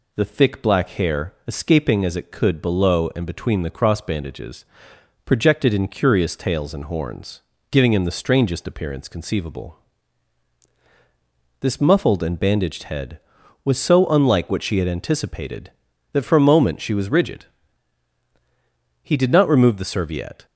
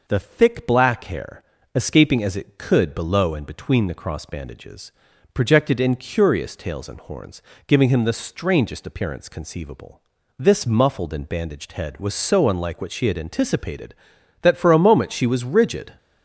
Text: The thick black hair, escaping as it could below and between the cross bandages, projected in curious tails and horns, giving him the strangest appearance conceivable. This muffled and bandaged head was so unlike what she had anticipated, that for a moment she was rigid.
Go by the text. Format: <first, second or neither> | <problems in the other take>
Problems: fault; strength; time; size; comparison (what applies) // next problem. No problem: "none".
second | goes on to say "He did not remove the serviette"; from 19.0 s on; 1.4 s long